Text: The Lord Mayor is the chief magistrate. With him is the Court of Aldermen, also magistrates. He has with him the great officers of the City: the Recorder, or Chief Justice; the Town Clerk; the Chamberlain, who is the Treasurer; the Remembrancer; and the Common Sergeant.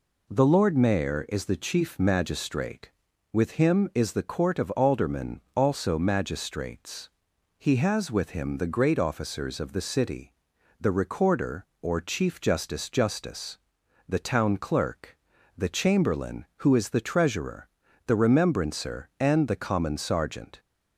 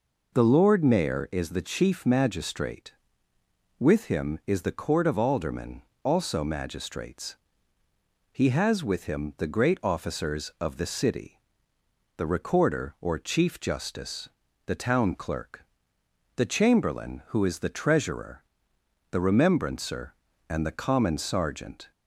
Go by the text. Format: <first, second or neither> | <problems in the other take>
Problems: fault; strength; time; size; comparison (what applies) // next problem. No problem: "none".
second | says "Justice" twice; at 12.8 s